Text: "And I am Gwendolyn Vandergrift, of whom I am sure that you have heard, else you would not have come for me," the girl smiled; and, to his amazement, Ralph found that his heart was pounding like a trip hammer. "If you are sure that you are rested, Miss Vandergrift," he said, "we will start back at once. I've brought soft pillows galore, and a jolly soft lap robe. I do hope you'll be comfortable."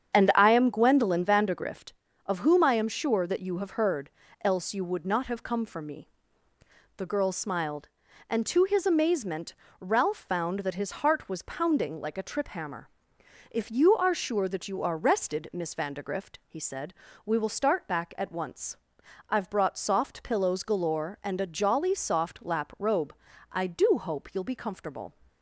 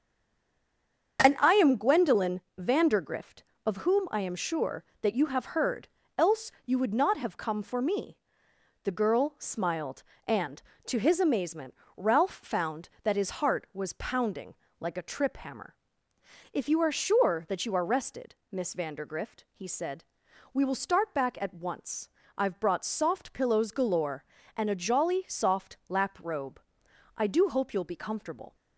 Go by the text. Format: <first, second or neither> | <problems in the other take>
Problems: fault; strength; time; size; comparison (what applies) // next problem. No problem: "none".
first | stays silent before the first word; noticeable; until 1.1 s; 1.1 s long // starts louder than the rest; until 2.2 s; 7 dB; strong in the first // pauses between "Gwendolyn" and "Vandergrift"; slight; at 2.4 s; 0.18 s long // pauses between "pounding" and "like"; slight; at 14.5 s; 0.24 s long